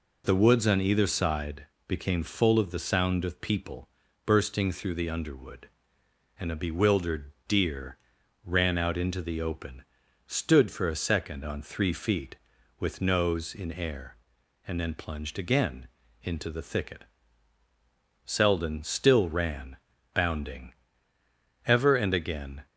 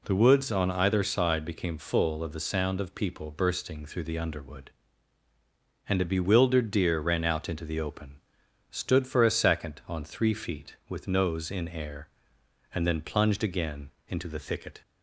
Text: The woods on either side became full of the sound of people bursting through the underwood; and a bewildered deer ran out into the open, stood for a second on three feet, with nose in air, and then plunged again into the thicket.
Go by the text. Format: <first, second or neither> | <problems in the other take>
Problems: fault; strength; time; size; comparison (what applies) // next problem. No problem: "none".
second | pauses between "side" and "became"; slight; at 1.6 s; 0.20 s long // pauses between "people" and "bursting"; at 3.8 s; 0.38 s long // pauses between "bewildered" and "deer"; slight; at 7.3 s; 0.16 s long // pauses between "deer" and "ran"; noticeable; at 7.9 s; 0.46 s long // pauses between "again" and "into"; slight; at 15.8 s; 0.36 s long; slight in the second // goes on to say "Selden still ran bounding ever and again"; strong; from 18.2 s on; 4.4 s long